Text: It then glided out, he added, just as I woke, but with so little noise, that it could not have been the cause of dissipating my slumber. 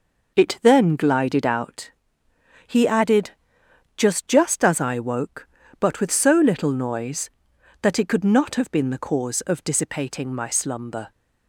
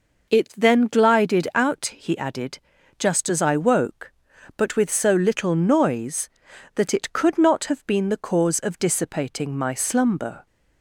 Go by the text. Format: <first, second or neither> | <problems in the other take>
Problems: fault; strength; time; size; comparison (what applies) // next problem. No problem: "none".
second | says "just" twice; at 4.2 s